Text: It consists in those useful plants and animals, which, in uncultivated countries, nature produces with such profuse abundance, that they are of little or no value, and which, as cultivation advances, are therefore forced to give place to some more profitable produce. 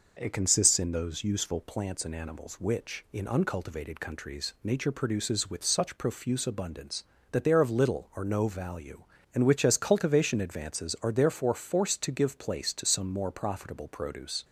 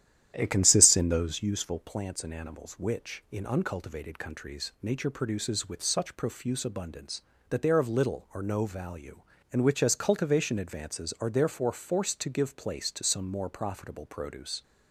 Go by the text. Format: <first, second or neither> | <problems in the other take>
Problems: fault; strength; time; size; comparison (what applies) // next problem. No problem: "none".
first | starts louder than the rest; strong; until 1.6 s; 11 dB